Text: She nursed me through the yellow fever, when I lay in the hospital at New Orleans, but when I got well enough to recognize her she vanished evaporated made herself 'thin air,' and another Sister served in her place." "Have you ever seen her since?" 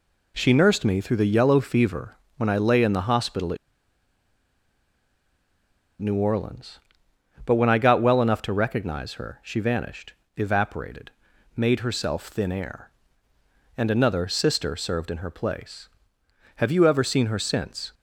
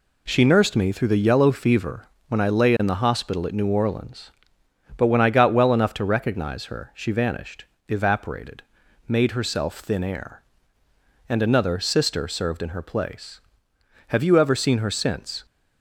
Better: second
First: pauses between "at" and "New"; strong; at 3.5 s; 2.4 s long // pauses between "vanished" and "evaporated"; slight; at 10.1 s; 0.22 s long // pauses between "evaporated" and "made"; noticeable; at 11.0 s; 0.46 s long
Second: pauses between "vanished" and "evaporated"; slight; at 7.6 s; 0.22 s long // pauses between "evaporated" and "made"; noticeable; at 8.6 s; 0.46 s long

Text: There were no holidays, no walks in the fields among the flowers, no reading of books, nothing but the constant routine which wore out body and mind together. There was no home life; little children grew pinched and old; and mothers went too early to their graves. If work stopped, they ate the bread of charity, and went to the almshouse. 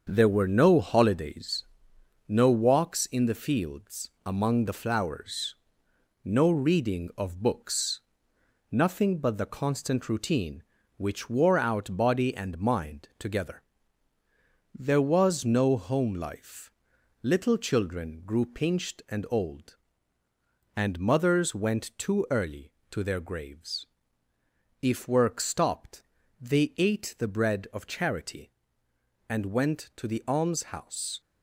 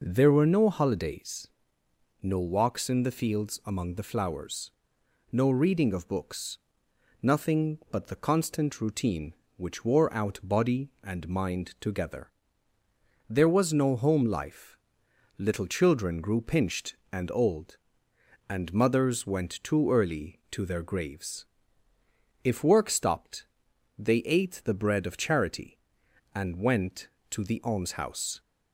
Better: second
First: gets quieter; throughout; 6.5 dB // pauses between "fields" and "among"; slight; at 4.0 s; 0.16 s long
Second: none

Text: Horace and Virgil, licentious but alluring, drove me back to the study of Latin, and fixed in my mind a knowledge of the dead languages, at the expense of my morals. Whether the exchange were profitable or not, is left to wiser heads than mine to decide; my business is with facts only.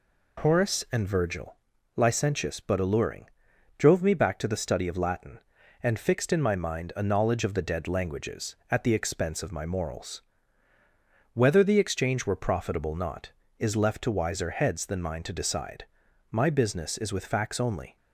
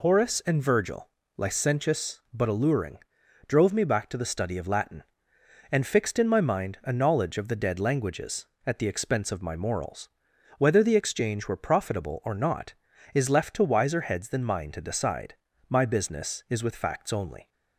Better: second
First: skips "or"; at 12.9 s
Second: none

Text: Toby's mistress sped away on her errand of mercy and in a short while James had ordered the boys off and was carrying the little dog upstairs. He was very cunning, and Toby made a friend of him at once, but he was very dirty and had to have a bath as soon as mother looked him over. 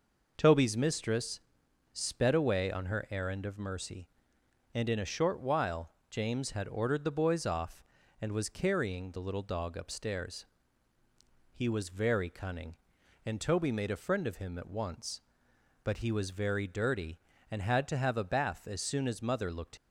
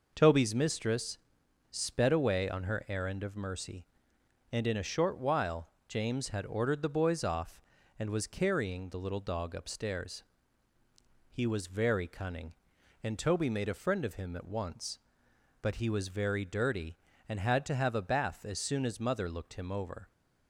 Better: second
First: pauses between "mistress" and "sped"; noticeable; at 1.3 s; 0.54 s long // pauses between "while" and "James"; slight; at 5.9 s; 0.18 s long // stops before "him over"; at 19.7 s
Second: pauses between "mistress" and "sped"; noticeable; at 1.1 s; 0.54 s long // pauses between "while" and "James"; slight; at 5.6 s; 0.18 s long

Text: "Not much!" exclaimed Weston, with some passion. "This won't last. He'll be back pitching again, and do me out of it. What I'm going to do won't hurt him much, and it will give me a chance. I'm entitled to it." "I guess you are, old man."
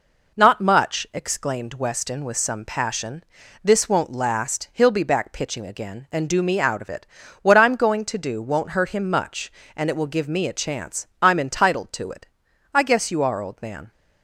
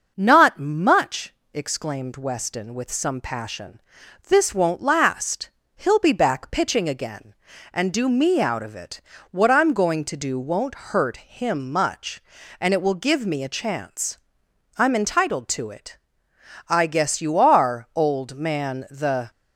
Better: first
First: none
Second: starts louder than the rest; noticeable; until 1.1 s; 6 dB // goes on to say "The"; slight; from 18.8 s on; 0.40 s long

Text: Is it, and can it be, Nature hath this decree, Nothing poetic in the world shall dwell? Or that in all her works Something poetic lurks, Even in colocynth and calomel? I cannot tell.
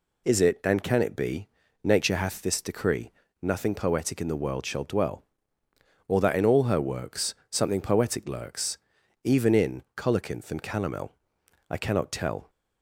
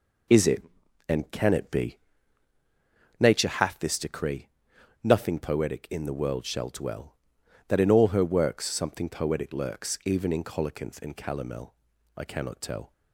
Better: first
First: none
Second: skips "Or"; at 7.4 s

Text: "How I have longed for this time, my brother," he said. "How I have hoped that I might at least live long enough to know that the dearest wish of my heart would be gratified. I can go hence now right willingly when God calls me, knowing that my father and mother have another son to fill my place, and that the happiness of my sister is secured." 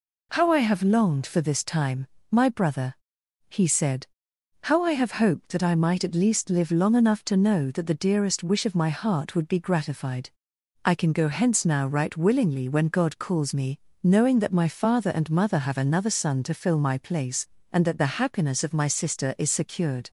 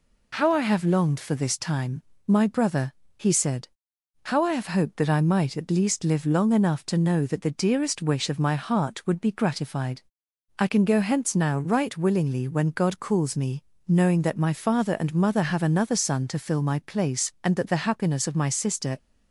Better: first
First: none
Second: stops before "is secured"; at 18.9 s

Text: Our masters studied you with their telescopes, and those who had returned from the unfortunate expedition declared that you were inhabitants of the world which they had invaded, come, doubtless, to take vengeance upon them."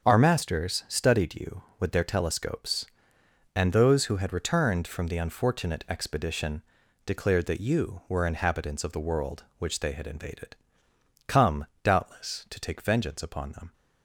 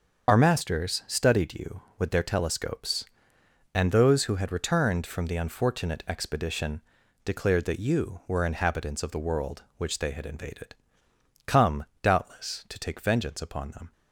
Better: first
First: starts louder than the rest; strong; until 1.1 s; 7.5 dB // pauses between "expedition" and "declared"; at 6.6 s; 0.44 s long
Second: loses the start of "Our"; at 0.2 s; 45 ms // starts louder than the rest; until 1.3 s; 7 dB // pauses between "expedition" and "declared"; at 6.7 s; 0.44 s long

